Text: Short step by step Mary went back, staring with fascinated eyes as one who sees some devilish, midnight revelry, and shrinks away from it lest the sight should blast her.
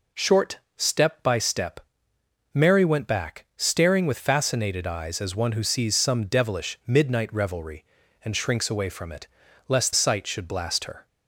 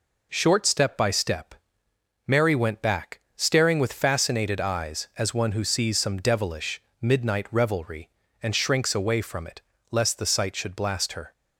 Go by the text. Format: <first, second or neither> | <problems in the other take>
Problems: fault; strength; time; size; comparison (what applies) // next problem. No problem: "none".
second | pauses between "Short" and "step"; slight; at 0.5 s; 0.18 s long // pauses between "step" and "Mary"; noticeable; at 1.8 s; 0.72 s long; noticeable in the second // pauses between "it" and "lest"; at 9.2 s; 0.42 s long; slight in the second // skips "the"; at 9.9 s